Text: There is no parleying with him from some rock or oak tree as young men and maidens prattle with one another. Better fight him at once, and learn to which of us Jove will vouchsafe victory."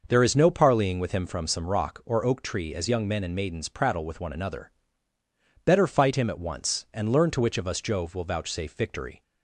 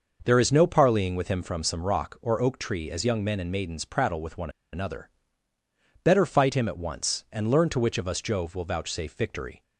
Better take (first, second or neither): first